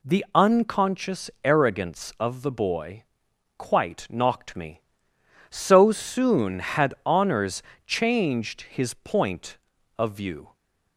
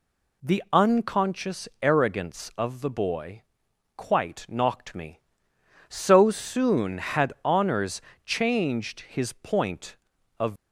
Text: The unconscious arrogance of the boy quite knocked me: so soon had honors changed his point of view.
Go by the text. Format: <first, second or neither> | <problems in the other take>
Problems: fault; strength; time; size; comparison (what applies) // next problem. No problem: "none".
first | pauses between "boy" and "quite"; noticeable; at 3.4 s; 0.56 s long; noticeable in the first // pauses between "honors" and "changed"; slight; at 7.9 s; 0.24 s long; slight in the first // stops before "view"; at 10.5 s